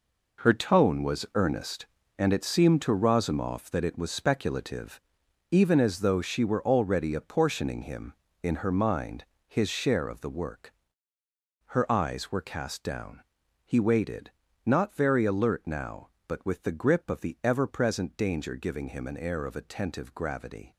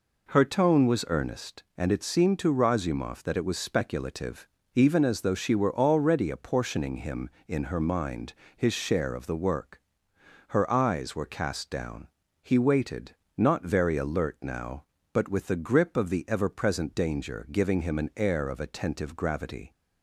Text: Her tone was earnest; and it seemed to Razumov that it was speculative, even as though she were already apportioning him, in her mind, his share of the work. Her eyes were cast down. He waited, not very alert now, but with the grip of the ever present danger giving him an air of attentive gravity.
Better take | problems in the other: second | gets quieter; strong; throughout; 10.5 dB

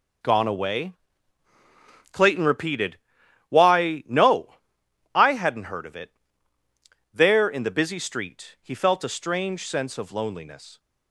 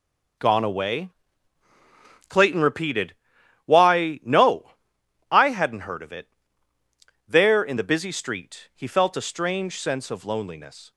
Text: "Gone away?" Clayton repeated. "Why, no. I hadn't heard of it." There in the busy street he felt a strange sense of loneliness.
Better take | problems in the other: neither | none

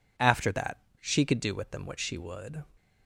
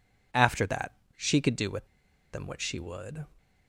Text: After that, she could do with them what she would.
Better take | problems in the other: first | pauses between "with" and "them"; noticeable; at 1.8 s; 0.46 s long

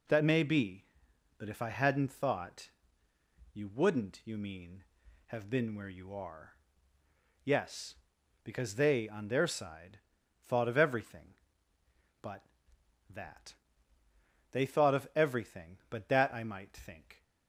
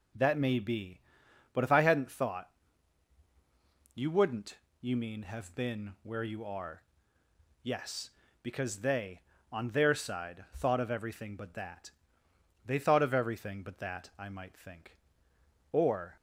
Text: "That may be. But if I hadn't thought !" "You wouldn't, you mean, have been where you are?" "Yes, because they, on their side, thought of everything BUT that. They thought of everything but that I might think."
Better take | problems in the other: first | goes on to say "Or"; slight; from 15.7 s on; 0.40 s long

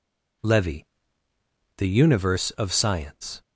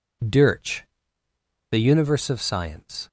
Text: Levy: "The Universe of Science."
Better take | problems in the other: first | says "Dirch" for "Levy"; at 0.2 s

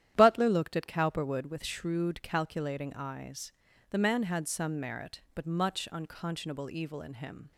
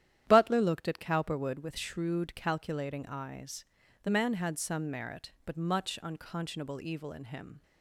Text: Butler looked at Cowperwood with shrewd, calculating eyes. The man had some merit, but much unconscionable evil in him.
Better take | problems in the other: neither | starts louder than the rest; strong; the same in both

